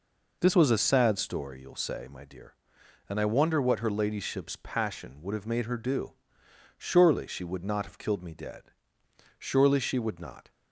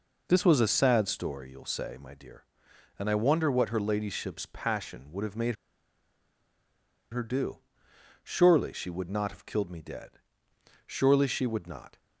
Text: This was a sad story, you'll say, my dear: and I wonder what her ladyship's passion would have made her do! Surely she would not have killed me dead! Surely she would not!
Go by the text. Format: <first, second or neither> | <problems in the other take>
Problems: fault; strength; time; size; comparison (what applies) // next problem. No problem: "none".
first | pauses between "made" and "her"; strong; at 5.5 s; 1.5 s long